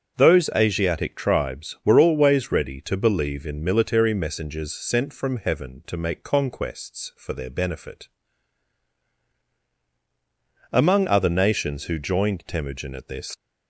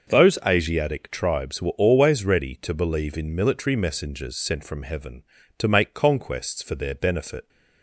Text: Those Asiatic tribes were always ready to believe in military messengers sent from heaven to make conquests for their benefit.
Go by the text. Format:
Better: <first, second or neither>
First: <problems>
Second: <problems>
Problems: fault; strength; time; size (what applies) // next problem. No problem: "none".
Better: second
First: starts louder than the rest; until 1.2 s; 6.5 dB // goes on to say "Among other nations who joined Temujin at this"; strong; from 10.7 s on; 2.6 s long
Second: none